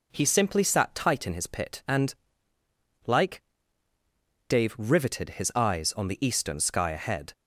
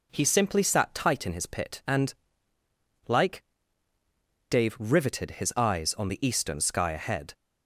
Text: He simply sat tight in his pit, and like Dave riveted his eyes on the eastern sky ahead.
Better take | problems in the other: neither | pauses between "and" and "like"; noticeable; the same in both // pauses between "like" and "Dave"; the same in both

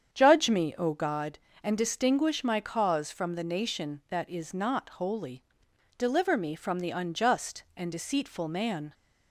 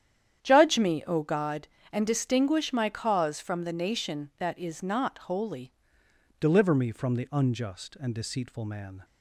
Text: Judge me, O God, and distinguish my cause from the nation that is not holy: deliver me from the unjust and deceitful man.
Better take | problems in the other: first | starts louder than the rest; strong; until 1.4 s; 9.5 dB; strong in the first // changes voice at "deliver"; from 6.4 s on; 2.6 s long

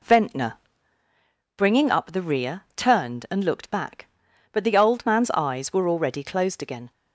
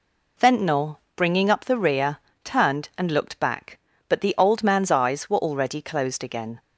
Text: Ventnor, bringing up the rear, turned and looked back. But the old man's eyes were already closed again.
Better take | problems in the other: neither | none

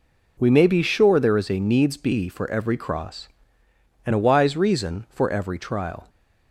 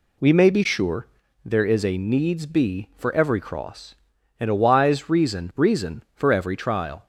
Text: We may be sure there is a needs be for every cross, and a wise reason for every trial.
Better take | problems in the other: first | pauses between "sure" and "there"; slight; at 1.0 s; 0.36 s long // says "reason" twice; at 5.5 s

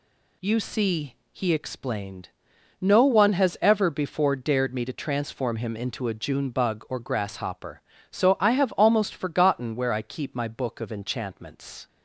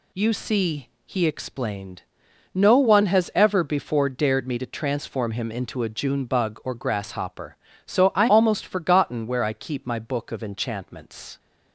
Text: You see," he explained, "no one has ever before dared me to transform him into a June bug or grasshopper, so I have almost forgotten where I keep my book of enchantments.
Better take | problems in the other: first | skips "have"; at 8.2 s

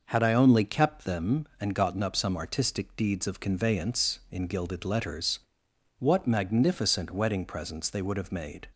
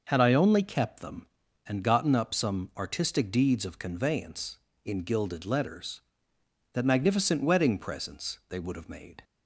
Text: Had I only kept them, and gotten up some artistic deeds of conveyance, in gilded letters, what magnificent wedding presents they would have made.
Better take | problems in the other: first | says "that" for "what"; at 6.7 s

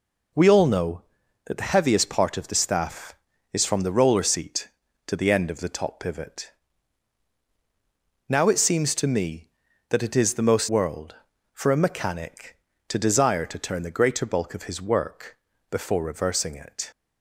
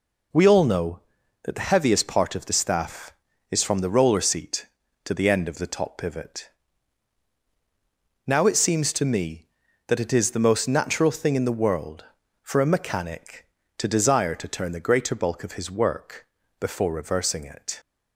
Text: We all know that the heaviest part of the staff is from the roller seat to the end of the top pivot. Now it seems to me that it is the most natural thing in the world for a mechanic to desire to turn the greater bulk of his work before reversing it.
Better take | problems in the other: second | skips "natural thing in the"; at 10.6 s // pauses between "work" and "before"; slight; at 15.3 s; 0.34 s long; slight in the second

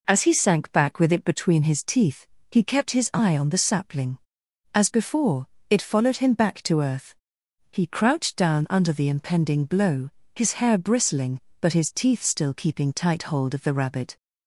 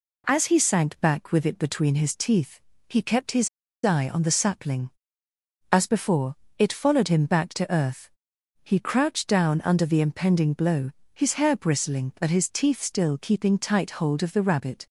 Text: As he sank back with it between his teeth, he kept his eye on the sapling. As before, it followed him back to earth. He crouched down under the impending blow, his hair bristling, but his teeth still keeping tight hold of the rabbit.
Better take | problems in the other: first | pauses between "his" and "eye"; at 3.4 s; 0.37 s long

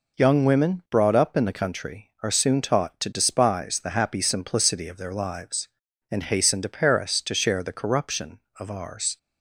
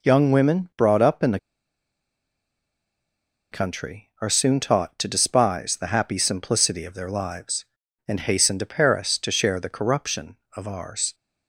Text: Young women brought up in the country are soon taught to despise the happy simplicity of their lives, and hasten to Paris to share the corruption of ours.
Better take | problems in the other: first | pauses between "the" and "country"; strong; at 1.3 s; 2.1 s long

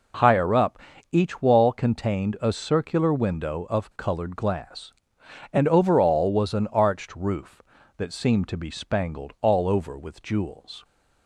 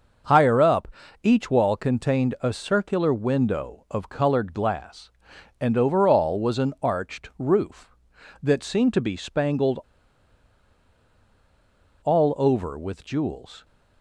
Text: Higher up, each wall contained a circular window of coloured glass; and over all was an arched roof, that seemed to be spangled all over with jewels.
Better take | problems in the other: first | starts louder than the rest; until 1.6 s; 6 dB // pauses between "spangled" and "all"; strong; at 9.7 s; 2.2 s long

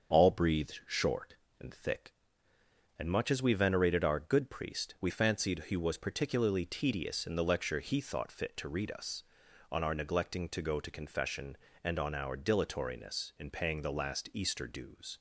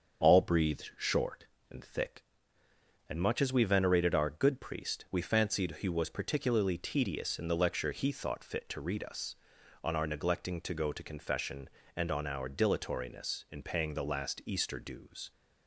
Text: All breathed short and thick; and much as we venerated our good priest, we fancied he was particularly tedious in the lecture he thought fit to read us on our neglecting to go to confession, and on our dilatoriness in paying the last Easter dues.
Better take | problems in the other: neither | starts louder than the rest; the same in both

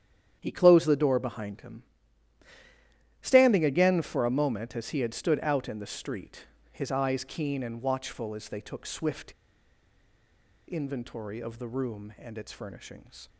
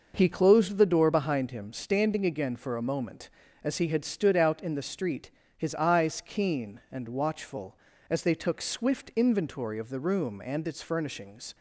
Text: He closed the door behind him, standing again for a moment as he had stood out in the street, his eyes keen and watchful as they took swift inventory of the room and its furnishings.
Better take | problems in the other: second | starts louder than the rest; strong; until 1.4 s; 9 dB // pauses between "swift" and "inventory"; strong; at 9.3 s; 1.3 s long

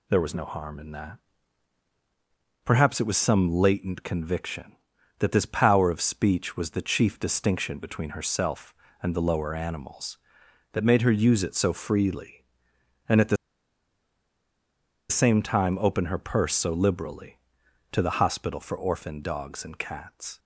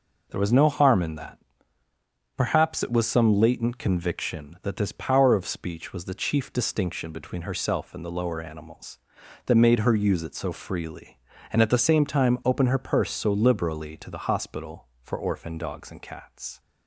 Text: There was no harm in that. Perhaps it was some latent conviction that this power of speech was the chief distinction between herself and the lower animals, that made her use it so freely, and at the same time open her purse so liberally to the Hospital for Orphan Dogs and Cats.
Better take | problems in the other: second | pauses between "the" and "same"; strong; at 13.3 s; 1.7 s long

